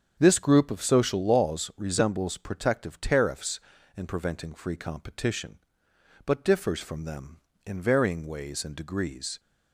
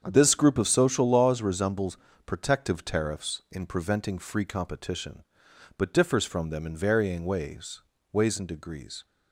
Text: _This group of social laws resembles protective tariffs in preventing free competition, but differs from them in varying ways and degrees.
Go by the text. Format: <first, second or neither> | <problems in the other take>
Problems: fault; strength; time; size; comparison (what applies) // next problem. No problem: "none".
first | starts louder than the rest; strong; until 1.0 s; 7.5 dB; strong in the first // pauses between "resembles" and "protective"; slight; at 1.9 s; 0.28 s long // says "ways" twice; at 8.1 s